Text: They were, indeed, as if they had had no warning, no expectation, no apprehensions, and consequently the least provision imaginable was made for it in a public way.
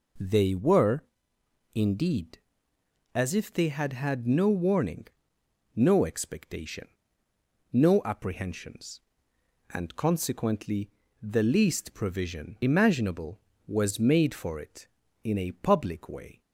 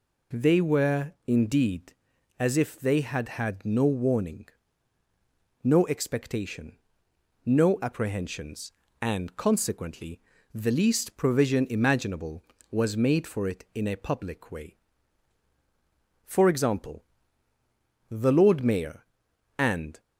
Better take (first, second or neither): first